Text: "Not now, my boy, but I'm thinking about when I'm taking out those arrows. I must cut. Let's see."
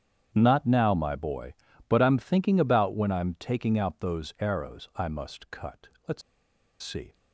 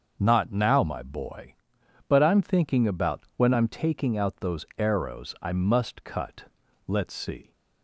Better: second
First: starts louder than the rest; strong; until 1.3 s; 9 dB // pauses between "Let's" and "see"; noticeable; at 6.2 s; 0.61 s long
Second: starts louder than the rest; until 1.2 s; 6.5 dB

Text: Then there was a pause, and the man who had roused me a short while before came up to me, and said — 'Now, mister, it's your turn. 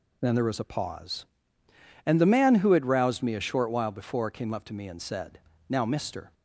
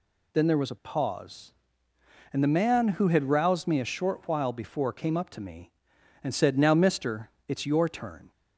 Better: second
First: stops before "it's your turn"; at 6.3 s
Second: none

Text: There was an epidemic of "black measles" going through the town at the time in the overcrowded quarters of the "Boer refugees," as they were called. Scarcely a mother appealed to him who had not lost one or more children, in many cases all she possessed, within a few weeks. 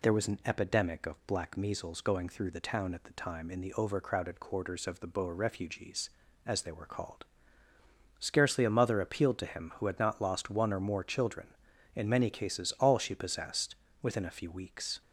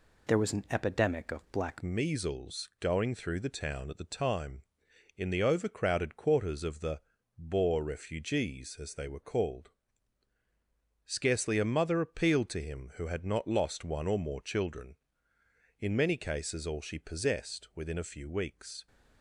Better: first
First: none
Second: changes voice at "measles"; from 1.8 s on; 17.0 s long // pauses between "the" and "Boer"; at 7.0 s; 0.38 s long

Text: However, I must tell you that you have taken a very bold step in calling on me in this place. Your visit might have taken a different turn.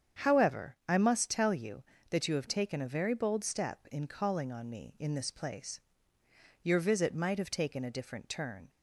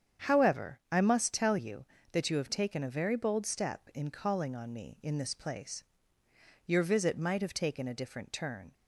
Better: neither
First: starts louder than the rest; strong; until 1.3 s; 8 dB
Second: starts louder than the rest; strong; until 1.3 s; 8 dB

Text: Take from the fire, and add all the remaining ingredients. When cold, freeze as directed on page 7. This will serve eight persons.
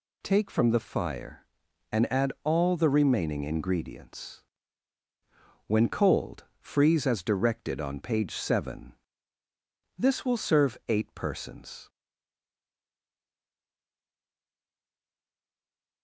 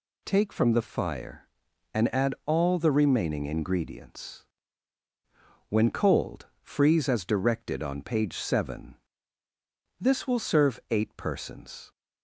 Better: second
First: stays silent after the last word; strong; from 11.8 s on; 4.2 s long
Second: none

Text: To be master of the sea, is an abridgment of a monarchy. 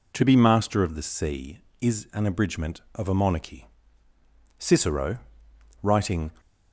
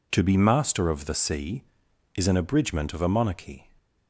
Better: second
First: goes on to say "Cicero writing"; strong; from 4.5 s on; 1.7 s long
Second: none

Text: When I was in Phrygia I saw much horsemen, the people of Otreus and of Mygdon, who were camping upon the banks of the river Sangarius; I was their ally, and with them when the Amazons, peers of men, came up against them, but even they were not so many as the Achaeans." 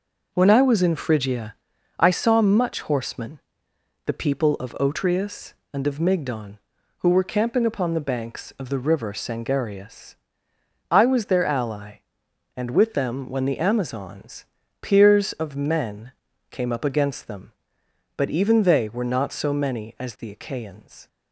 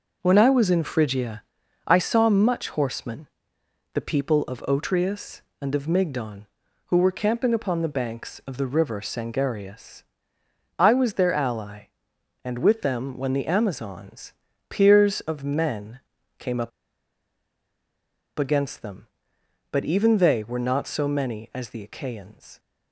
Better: first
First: pauses between "Phrygia" and "I"; at 1.5 s; 0.44 s long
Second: pauses between "Phrygia" and "I"; at 1.4 s; 0.44 s long // pauses between "up" and "against"; strong; at 16.7 s; 1.6 s long

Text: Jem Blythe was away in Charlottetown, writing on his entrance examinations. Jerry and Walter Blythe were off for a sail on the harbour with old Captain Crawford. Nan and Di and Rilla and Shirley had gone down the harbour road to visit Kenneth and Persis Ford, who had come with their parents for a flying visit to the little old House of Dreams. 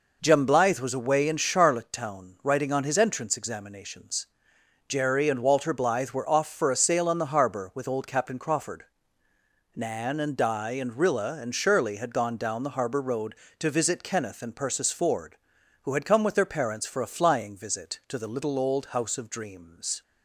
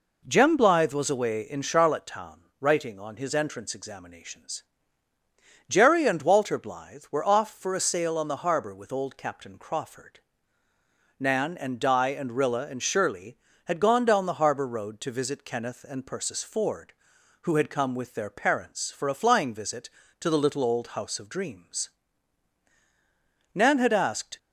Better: first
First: none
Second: goes on to say "Nan had asked"; noticeable; from 23.5 s on; 0.84 s long

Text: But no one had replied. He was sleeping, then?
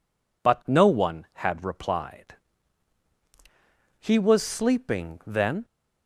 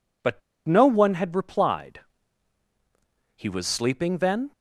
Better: first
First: none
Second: pauses between "But" and "no"; slight; at 0.4 s; 0.27 s long

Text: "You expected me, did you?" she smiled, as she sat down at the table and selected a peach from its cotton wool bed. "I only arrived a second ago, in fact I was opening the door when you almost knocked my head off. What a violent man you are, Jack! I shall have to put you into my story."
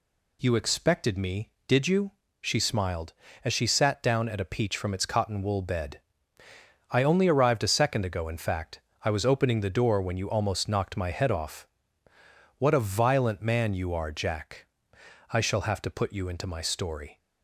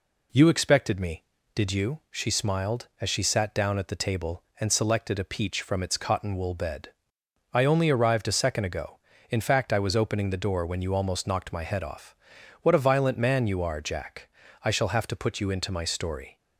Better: second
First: skips "the table and selected"; at 4.4 s // pauses between "fact" and "I"; slight; at 8.8 s; 0.22 s long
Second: none

